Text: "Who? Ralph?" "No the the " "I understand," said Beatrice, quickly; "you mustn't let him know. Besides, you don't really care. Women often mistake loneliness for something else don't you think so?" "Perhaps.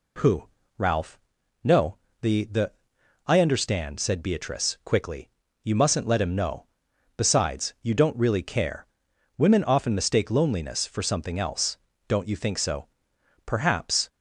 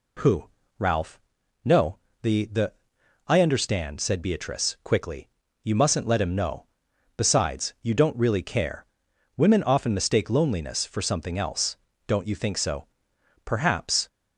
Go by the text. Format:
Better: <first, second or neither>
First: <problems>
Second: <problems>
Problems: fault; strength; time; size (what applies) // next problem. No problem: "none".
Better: neither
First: pauses between "No" and "the"; slight; at 1.9 s; 0.24 s long // pauses between "else" and "don't"; slight; at 11.7 s; 0.32 s long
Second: pauses between "No" and "the"; slight; at 1.9 s; 0.24 s long // pauses between "else" and "don't"; slight; at 11.7 s; 0.32 s long